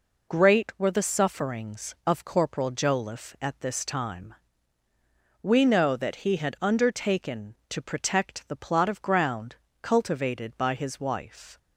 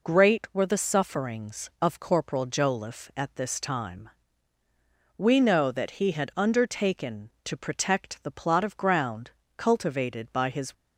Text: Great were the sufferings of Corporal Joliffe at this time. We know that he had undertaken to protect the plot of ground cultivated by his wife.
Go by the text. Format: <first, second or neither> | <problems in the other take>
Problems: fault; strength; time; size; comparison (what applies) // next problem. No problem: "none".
first | pauses between "ground" and "cultivated"; slight; at 9.3 s; 0.26 s long; slight in the first // stops before "wife"; at 10.7 s